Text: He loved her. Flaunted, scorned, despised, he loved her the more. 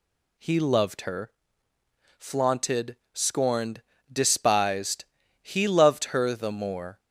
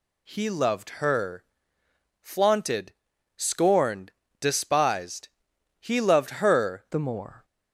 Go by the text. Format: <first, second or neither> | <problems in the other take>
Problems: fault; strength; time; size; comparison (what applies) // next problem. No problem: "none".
first | changes voice at "the"; from 6.9 s on; 0.5 s long